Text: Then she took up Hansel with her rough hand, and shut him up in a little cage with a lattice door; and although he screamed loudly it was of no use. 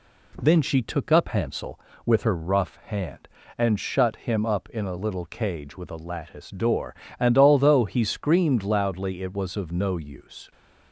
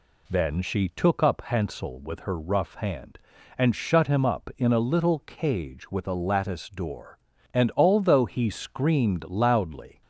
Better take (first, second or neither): first